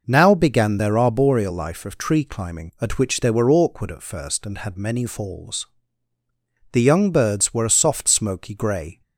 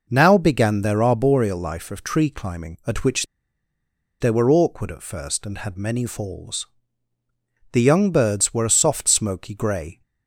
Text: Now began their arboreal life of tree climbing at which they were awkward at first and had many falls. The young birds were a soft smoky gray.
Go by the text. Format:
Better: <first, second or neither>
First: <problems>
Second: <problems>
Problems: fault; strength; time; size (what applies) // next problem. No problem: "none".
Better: first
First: none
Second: pauses between "which" and "they"; noticeable; at 3.2 s; 0.95 s long